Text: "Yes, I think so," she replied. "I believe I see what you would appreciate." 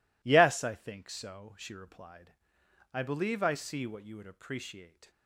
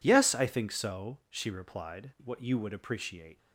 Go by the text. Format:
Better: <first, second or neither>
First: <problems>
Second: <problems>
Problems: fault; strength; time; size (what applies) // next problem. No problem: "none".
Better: first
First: none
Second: skips "I believe I see"; at 2.1 s